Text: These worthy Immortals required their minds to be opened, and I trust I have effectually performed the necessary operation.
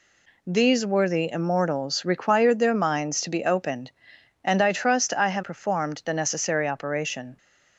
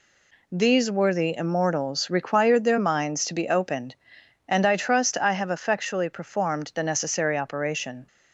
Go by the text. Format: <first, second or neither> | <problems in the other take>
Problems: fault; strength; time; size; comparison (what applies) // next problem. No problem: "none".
second | skips "effectually"; at 5.4 s